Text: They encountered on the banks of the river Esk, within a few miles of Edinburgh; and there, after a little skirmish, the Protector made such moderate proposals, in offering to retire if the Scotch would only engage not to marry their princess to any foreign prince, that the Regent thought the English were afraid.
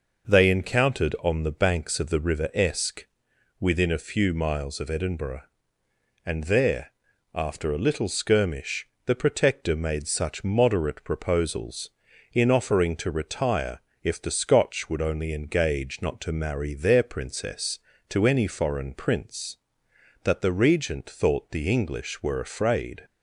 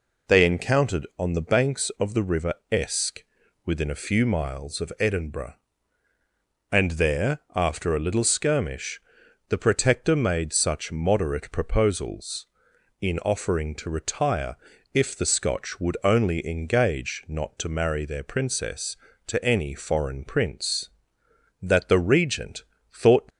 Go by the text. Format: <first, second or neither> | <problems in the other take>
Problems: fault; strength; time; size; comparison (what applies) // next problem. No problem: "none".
first | pauses between "river" and "Esk"; slight; at 2.5 s; 0.18 s long // pauses between "retire" and "if"; at 14.5 s; 0.40 s long; slight in the first // pauses between "Regent" and "thought"; slight; at 22.6 s; 0.30 s long // stops before "the English were afraid"; at 23.3 s